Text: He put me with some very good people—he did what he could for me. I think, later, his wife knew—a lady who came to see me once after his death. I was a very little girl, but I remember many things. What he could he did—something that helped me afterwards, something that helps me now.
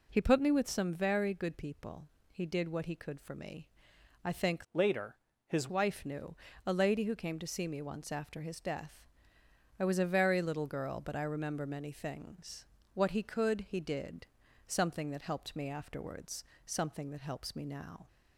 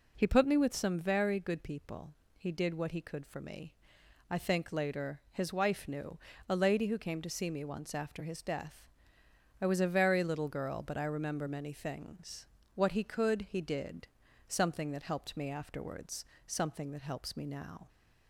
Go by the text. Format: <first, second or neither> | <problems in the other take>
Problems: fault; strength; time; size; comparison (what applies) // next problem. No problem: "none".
second | changes voice from "later" to "his"; from 4.7 to 5.6 s; 0.9 s long